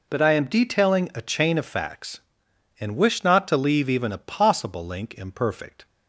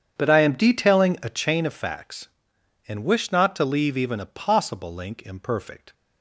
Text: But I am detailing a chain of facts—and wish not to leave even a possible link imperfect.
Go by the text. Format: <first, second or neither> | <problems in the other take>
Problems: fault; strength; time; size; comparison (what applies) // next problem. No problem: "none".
first | starts louder than the rest; strong; until 1.5 s; 8 dB